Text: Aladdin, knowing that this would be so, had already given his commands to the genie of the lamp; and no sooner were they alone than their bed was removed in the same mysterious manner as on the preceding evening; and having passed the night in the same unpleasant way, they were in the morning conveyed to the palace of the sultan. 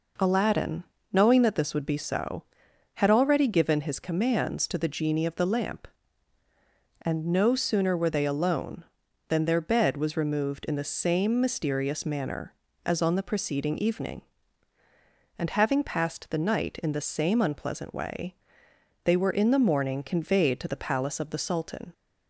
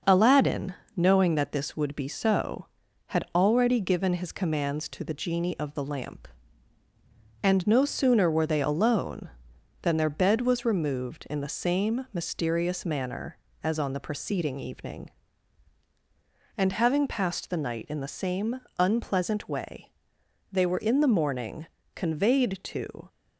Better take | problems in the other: first | starts louder than the rest; noticeable; until 1.2 s; 6 dB // pauses between "same" and "unpleasant"; slight; at 18.5 s; 0.18 s long // pauses between "morning" and "conveyed"; slight; at 21.6 s; 0.28 s long // stops before "the palace of the sultan"; at 23.0 s

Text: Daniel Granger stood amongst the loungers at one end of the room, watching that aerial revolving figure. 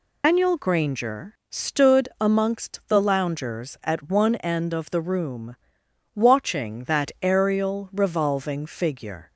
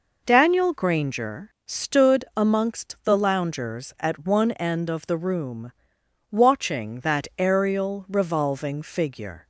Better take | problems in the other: second | loses the start of "Daniel"; at 0.2 s; 155 ms

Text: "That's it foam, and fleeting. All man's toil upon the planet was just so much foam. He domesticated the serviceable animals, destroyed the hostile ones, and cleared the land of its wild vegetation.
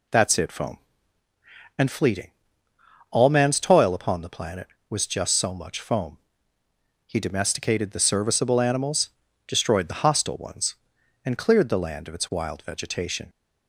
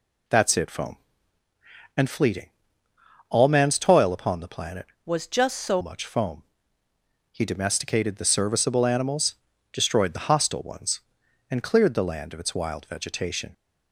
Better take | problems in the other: first | changes voice from "was" to "so"; from 5.0 to 5.8 s; 0.8 s long

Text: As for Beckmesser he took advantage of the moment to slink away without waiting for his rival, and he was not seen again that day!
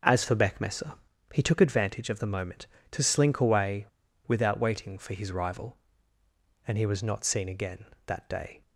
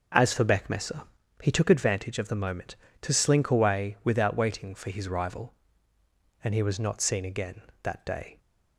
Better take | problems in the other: second | pauses between "Beckmesser" and "he"; slight; at 0.9 s; 0.36 s long; slight in the second // pauses between "away" and "without"; at 3.8 s; 0.41 s long

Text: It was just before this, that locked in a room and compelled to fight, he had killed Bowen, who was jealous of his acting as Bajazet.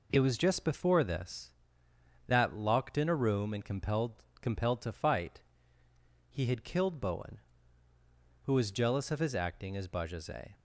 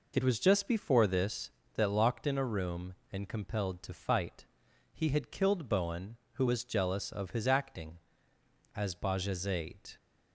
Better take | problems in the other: second | says "compelled" twice; at 4.4 s

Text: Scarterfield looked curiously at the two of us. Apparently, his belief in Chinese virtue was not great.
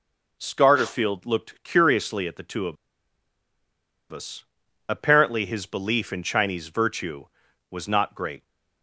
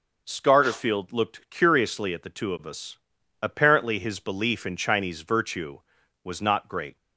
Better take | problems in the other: second | pauses between "of" and "us"; strong; at 2.7 s; 1.3 s long

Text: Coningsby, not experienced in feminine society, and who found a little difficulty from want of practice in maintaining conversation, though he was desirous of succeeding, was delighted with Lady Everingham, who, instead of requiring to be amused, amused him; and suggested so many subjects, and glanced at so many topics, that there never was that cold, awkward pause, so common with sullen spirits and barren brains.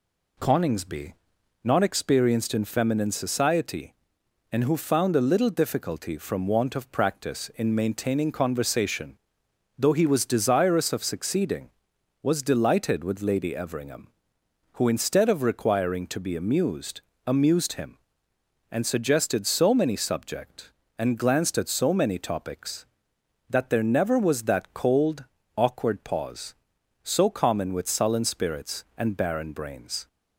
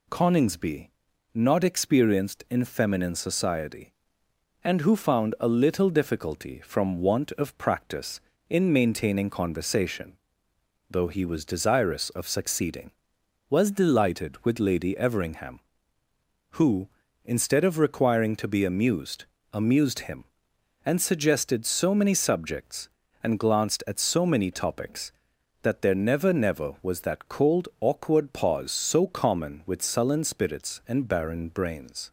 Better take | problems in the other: first | says "never" twice; at 26.3 s

